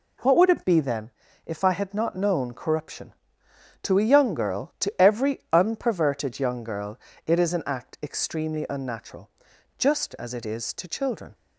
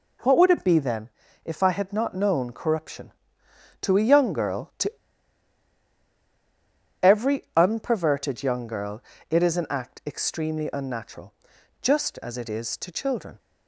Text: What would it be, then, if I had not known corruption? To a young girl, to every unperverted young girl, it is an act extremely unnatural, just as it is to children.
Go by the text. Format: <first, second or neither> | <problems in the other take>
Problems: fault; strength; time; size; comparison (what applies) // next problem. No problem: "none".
first | pauses between "to" and "every"; strong; at 4.9 s; 2.0 s long